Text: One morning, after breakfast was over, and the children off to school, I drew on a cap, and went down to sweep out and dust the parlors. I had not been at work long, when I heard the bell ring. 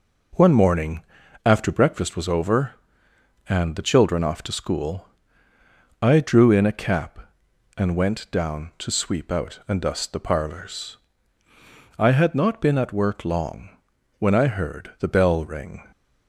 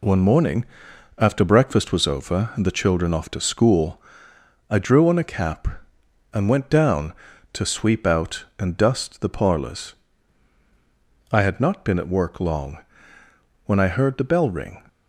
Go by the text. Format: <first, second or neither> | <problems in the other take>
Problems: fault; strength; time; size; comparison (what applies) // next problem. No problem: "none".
second | says "in" for "on"; at 6.4 s